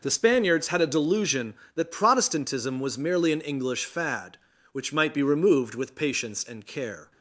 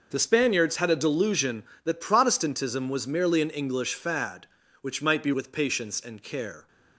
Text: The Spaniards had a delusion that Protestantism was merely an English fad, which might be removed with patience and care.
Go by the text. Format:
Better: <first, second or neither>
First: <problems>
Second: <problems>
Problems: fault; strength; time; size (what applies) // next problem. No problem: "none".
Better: first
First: none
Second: skips "removed"; at 5.3 s